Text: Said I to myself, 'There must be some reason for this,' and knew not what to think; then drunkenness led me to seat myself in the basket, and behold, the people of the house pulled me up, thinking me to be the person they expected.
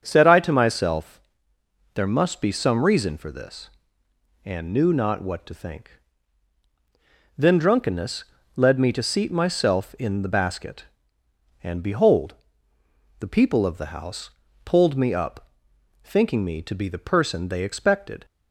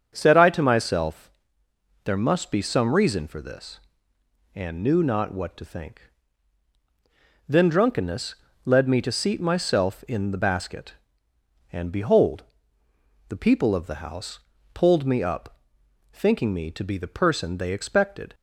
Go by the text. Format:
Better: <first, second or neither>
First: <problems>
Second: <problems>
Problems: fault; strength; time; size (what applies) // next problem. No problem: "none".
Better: neither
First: starts louder than the rest; strong; until 1.0 s; 7.5 dB // pauses between "drunkenness" and "led"; slight; at 8.2 s; 0.32 s long // pauses between "house" and "pulled"; slight; at 14.3 s; 0.34 s long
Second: starts louder than the rest; strong; until 1.1 s; 7.5 dB // pauses between "drunkenness" and "led"; slight; at 8.3 s; 0.30 s long // pauses between "house" and "pulled"; slight; at 14.3 s; 0.34 s long